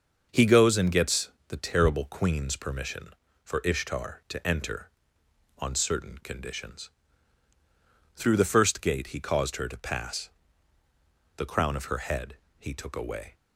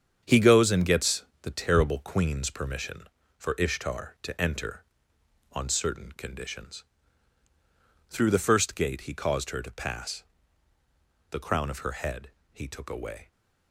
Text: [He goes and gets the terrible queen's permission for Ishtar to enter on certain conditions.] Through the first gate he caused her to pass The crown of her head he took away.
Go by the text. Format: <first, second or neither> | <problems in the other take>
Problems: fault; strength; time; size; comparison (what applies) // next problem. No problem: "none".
first | gets quieter; strong; throughout; 7 dB // starts louder than the rest; strong; until 1.2 s; 8 dB; also in the first // pauses between "gets" and "the"; slight; at 1.2 s; 0.16 s long; slight in the first // pauses between "pass" and "The"; at 10.2 s; 1.0 s long; also in the first // pauses between "head" and "he"; slight; at 12.2 s; 0.24 s long; slight in the first